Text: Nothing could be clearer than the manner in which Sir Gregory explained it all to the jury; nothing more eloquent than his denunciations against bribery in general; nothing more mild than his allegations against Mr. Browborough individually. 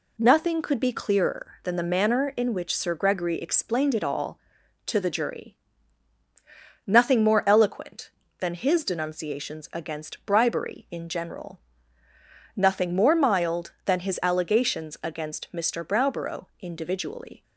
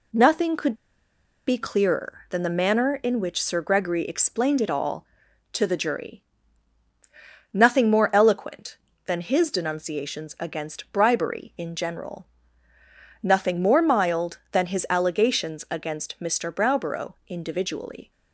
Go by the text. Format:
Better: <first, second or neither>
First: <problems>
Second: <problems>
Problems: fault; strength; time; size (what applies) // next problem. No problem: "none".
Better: first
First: pauses between "Browborough" and "individually"; slight; at 16.4 s; 0.16 s long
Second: pauses between "could" and "be"; noticeable; at 0.7 s; 0.73 s long // pauses between "Browborough" and "individually"; slight; at 17.1 s; 0.16 s long